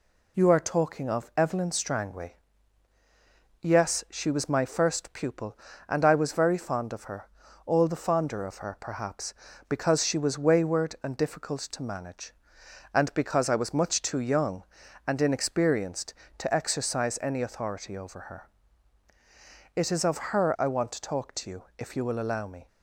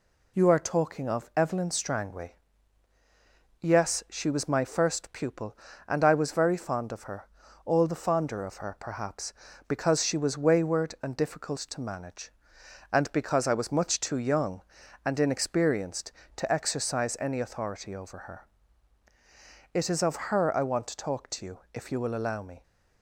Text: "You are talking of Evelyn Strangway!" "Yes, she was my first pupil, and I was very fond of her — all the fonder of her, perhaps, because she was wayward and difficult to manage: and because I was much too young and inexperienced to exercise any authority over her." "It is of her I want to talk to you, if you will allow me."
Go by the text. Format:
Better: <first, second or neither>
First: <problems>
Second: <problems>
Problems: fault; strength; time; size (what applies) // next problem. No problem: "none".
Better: neither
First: none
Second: none